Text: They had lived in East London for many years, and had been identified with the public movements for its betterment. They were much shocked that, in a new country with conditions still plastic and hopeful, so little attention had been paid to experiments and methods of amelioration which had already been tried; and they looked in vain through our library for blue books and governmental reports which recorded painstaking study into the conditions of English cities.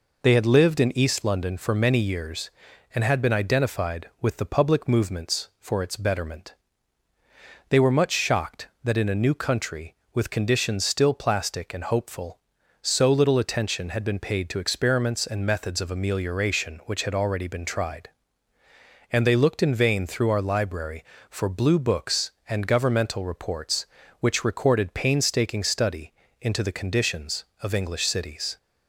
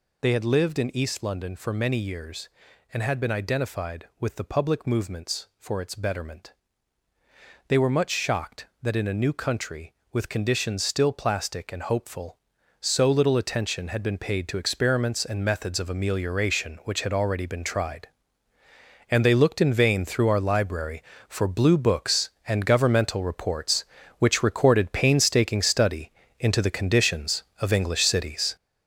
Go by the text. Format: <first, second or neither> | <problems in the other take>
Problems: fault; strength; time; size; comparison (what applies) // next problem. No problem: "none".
first | gets louder; strong; throughout; 7.5 dB // pauses between "study" and "into"; slight; at 26.0 s; 0.30 s long; slight in the first